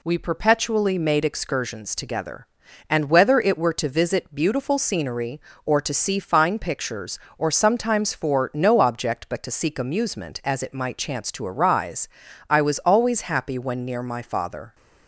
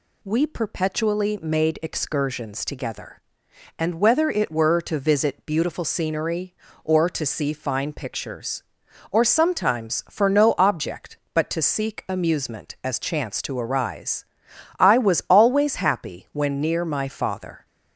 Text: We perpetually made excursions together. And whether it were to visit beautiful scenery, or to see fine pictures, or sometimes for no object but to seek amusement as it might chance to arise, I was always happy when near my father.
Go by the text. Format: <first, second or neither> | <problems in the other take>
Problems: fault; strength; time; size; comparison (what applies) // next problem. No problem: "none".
first | skips "it might"; at 12.9 s